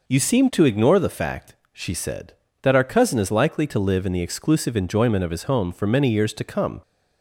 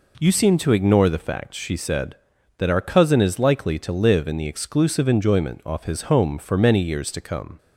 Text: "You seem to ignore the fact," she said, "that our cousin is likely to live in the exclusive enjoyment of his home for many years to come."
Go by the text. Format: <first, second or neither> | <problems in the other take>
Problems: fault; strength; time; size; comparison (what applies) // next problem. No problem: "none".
first | says "off" for "of"; at 5.6 s